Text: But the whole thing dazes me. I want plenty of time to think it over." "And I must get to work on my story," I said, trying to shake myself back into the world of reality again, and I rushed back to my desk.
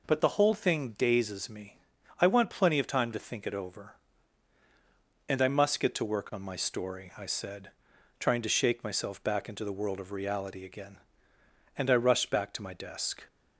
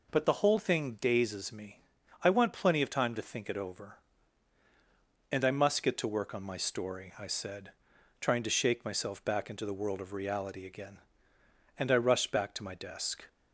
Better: neither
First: none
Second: none

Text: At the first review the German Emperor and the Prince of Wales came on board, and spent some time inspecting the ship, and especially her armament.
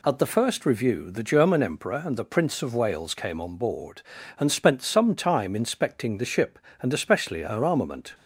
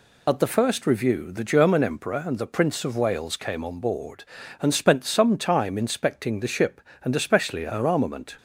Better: first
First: none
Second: loses the start of "At"; at 0.2 s; 35 ms

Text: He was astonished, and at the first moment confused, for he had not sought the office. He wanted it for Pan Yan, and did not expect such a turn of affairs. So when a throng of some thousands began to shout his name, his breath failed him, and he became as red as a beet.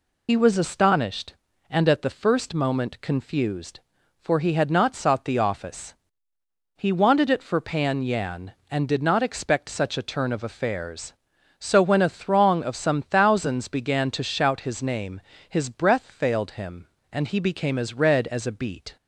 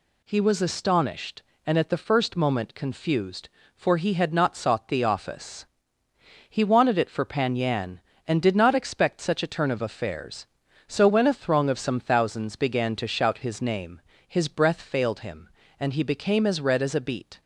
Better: second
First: loses the start of "He"; at 0.2 s; 65 ms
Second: none

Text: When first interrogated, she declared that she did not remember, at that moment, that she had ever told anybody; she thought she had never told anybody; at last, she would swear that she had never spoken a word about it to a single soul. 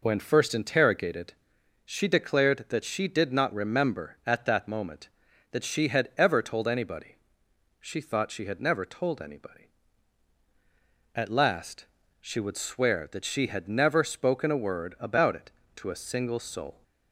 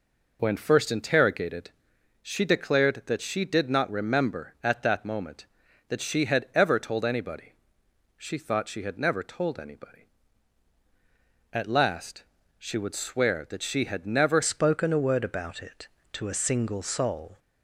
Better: first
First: none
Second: changes voice at "spoken"; from 14.4 s on; 2.9 s long

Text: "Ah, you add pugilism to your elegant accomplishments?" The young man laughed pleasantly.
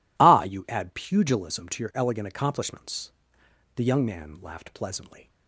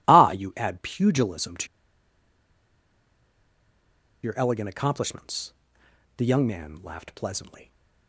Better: first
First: none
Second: pauses between "to" and "your"; strong; at 1.6 s; 2.5 s long

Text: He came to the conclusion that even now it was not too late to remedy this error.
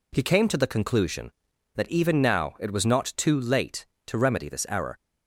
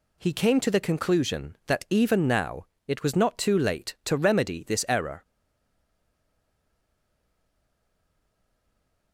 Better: first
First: none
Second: pauses between "now" and "it"; slight; at 2.6 s; 0.22 s long // stays silent after the last word; strong; from 5.2 s on; 3.9 s long

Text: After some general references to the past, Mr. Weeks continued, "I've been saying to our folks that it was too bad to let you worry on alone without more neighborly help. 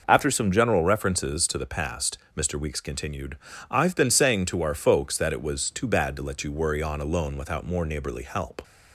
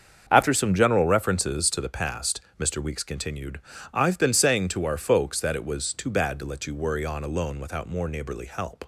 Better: first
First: none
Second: gets quieter; strong; throughout; 9.5 dB

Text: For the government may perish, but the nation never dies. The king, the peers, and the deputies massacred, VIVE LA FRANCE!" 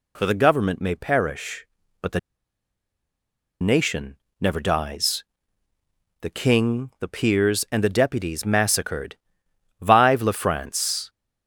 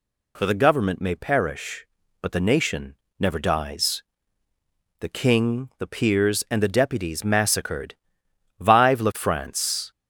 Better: second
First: pauses between "the" and "nation"; strong; at 2.1 s; 1.4 s long // pauses between "nation" and "never"; slight; at 4.1 s; 0.22 s long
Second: pauses between "nation" and "never"; slight; at 2.9 s; 0.22 s long

